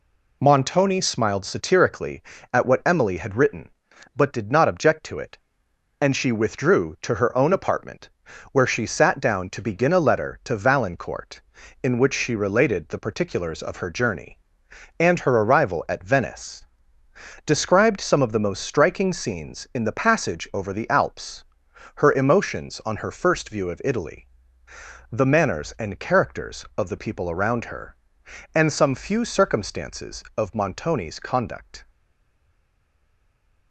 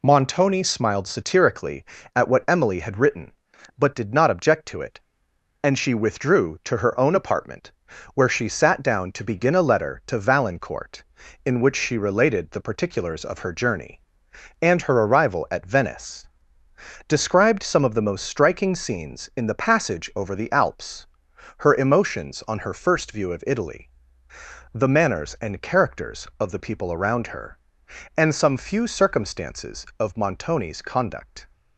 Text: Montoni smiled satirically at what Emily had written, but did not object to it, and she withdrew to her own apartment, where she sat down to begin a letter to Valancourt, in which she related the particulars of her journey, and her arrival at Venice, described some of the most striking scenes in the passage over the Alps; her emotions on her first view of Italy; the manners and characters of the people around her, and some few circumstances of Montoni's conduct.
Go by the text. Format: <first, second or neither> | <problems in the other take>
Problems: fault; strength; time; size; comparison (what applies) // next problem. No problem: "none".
second | stays silent after the last word; noticeable; from 31.9 s on; 1.8 s long